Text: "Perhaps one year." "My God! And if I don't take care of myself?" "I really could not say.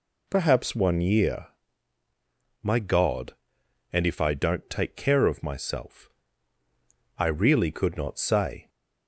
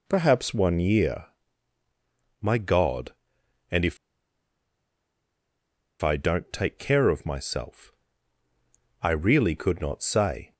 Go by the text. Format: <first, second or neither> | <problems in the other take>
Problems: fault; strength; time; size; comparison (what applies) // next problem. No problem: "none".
first | pauses between "if" and "I"; strong; at 3.9 s; 2.0 s long